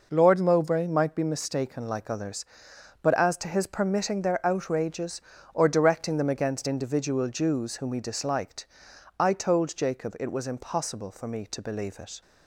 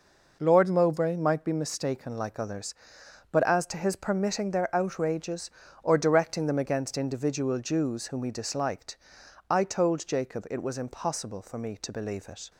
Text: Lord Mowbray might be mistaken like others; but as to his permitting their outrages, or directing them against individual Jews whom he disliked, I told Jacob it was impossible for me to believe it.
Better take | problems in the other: neither | none

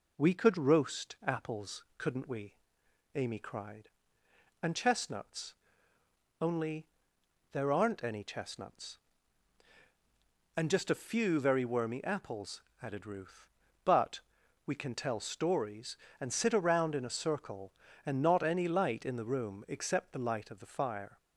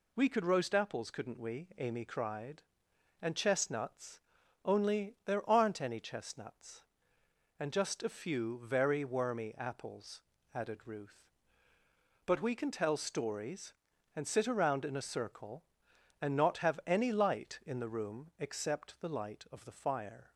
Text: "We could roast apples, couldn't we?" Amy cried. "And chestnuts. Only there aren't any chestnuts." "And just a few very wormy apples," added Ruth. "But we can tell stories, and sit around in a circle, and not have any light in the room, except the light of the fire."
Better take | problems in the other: second | pauses between "Only" and "there"; noticeable; at 6.8 s; 0.64 s long // pauses between "But" and "we"; noticeable; at 14.2 s; 0.46 s long // skips "have"; at 18.4 s

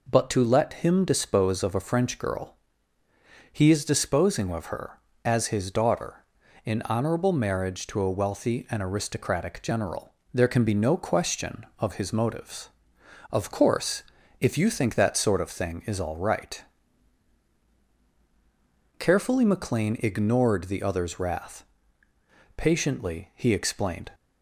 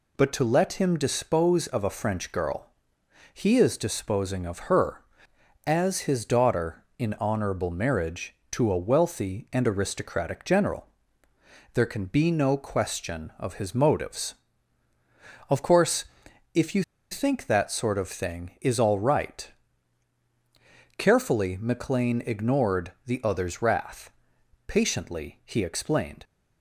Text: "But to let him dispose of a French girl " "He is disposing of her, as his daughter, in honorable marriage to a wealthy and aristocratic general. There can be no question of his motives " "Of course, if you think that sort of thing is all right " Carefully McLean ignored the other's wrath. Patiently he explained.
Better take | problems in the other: first | pauses between "you" and "think"; slight; at 16.8 s; 0.28 s long

